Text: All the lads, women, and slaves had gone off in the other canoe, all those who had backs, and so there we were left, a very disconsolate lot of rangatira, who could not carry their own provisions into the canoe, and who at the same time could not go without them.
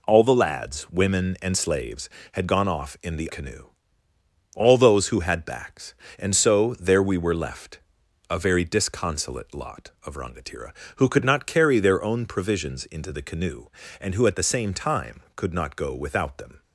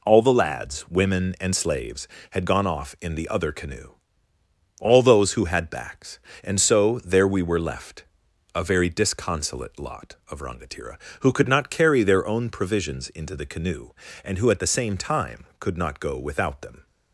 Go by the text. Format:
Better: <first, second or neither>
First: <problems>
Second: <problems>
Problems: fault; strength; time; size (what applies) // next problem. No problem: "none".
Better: second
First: skips "other"; at 3.2 s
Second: none